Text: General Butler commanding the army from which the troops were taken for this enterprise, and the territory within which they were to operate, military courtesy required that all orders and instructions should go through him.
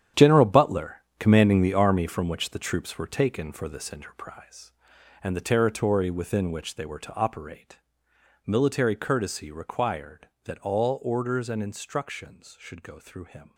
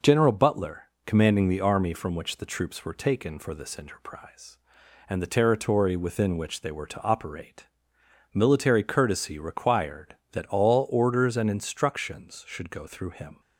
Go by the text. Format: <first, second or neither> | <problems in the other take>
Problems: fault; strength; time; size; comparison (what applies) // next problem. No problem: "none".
second | gets quieter; strong; throughout; 12 dB // pauses between "Butler" and "commanding"; slight; at 1.0 s; 0.16 s long; slight in the second